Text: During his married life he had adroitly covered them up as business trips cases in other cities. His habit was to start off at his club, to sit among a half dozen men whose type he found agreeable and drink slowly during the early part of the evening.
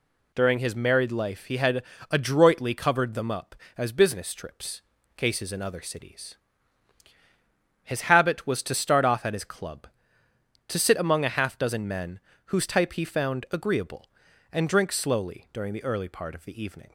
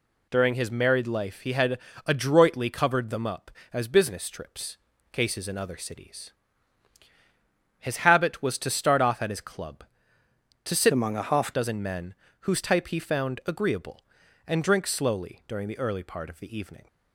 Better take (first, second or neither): first